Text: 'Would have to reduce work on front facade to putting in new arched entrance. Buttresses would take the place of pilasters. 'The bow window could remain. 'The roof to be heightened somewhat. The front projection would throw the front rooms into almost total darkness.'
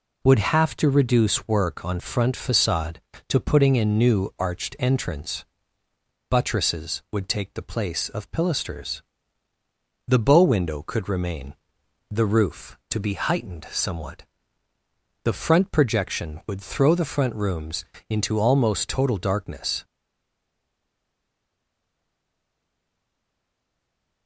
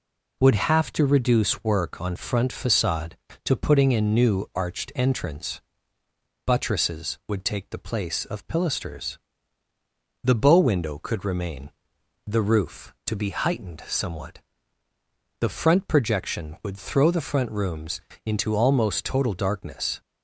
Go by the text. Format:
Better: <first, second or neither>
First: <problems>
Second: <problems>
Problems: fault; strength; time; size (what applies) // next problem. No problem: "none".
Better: second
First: pauses between "rooms" and "into"; slight; at 17.8 s; 0.24 s long // stays silent after the last word; strong; from 19.8 s on; 4.4 s long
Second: pauses between "rooms" and "into"; slight; at 17.9 s; 0.24 s long